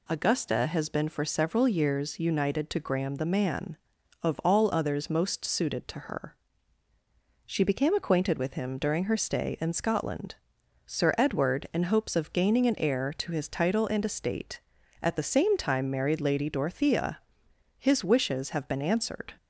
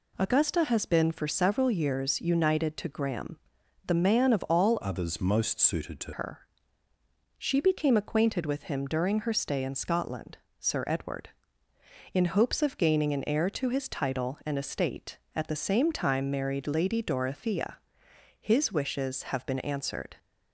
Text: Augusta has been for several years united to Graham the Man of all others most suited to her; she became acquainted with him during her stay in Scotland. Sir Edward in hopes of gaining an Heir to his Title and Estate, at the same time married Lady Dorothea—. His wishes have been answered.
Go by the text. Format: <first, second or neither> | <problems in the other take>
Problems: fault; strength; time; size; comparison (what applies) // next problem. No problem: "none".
first | pauses between "Graham" and "the"; noticeable; at 3.3 s; 0.48 s long // changes voice from "others" to "to"; from 4.8 to 6.1 s; 1.3 s long